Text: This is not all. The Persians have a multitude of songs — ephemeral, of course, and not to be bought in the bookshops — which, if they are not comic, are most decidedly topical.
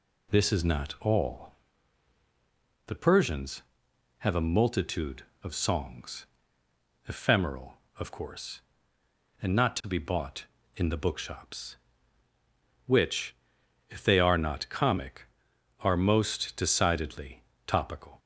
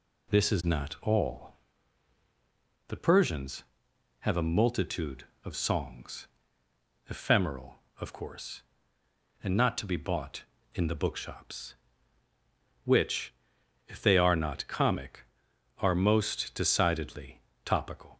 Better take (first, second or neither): neither